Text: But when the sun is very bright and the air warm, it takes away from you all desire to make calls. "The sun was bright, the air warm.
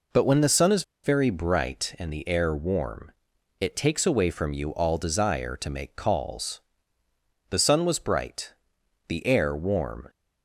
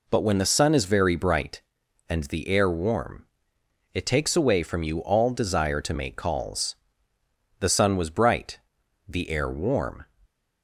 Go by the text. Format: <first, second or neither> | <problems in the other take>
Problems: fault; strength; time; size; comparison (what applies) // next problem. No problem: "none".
second | pauses between "is" and "very"; slight; at 0.8 s; 0.21 s long